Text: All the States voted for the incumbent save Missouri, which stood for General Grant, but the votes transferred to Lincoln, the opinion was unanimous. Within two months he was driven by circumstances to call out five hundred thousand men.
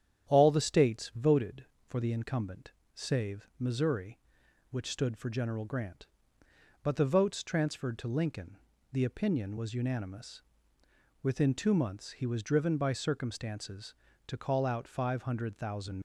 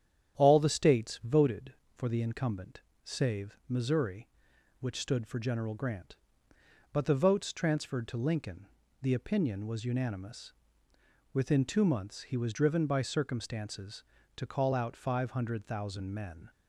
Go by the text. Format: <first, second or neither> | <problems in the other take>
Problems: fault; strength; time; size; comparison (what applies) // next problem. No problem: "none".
second | starts louder than the rest; strong; until 1.3 s; 10 dB; strong in the second // pauses between "incumbent" and "save"; slight; at 2.7 s; 0.24 s long; slight in the second // stops before "men"; at 15.9 s